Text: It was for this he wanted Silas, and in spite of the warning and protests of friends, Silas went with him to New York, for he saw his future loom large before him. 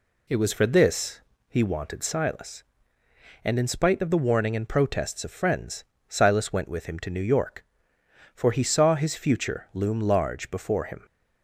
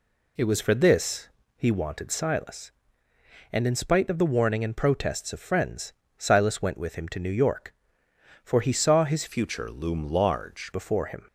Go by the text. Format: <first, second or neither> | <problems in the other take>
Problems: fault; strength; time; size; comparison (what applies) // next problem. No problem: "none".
first | pauses between "this" and "he"; slight; at 1.2 s; 0.28 s long; slight in the first // changes voice from "future" to "large"; from 9.2 to 10.7 s; 1.5 s long